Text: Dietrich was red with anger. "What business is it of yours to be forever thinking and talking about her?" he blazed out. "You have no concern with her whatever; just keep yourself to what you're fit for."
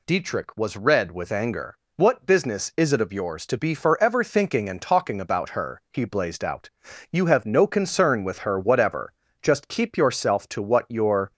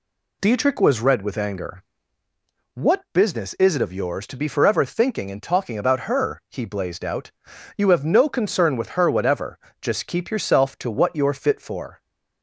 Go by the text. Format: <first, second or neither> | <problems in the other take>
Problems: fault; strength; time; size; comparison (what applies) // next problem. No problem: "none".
second | stops before "fit for"; at 11.3 s